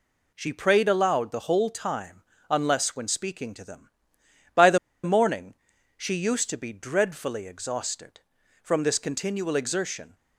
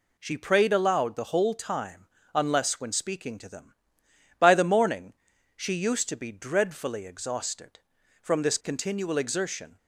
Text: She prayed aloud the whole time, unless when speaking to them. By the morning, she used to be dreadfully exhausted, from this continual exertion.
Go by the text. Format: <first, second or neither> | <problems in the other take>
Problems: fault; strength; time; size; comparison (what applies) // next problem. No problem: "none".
second | pauses between "the" and "morning"; slight; at 4.7 s; 0.26 s long